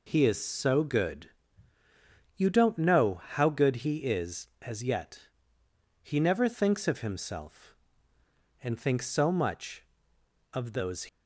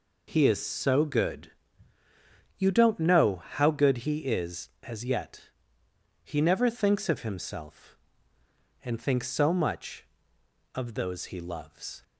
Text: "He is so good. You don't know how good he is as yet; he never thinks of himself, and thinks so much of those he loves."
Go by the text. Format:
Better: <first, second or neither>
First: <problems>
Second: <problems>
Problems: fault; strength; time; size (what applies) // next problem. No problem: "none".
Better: second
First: stops before "he loves"; at 11.0 s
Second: none